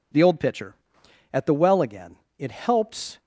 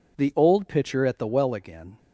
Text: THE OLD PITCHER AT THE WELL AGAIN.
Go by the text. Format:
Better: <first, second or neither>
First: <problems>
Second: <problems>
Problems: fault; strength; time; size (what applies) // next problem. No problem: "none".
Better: second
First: goes on to say "It helps"; noticeable; from 2.3 s on; 0.82 s long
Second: none